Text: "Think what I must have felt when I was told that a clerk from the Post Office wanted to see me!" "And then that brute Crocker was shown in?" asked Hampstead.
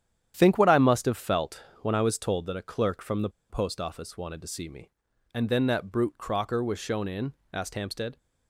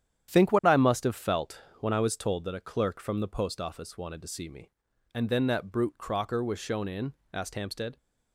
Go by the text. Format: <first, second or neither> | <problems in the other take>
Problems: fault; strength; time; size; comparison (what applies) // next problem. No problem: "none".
second | starts louder than the rest; strong; until 1.3 s; 10 dB; strong in the second // pauses between "felt" and "when"; slight; at 1.6 s; 0.18 s long; slight in the second // pauses between "the" and "Post"; slight; at 3.2 s; 0.20 s long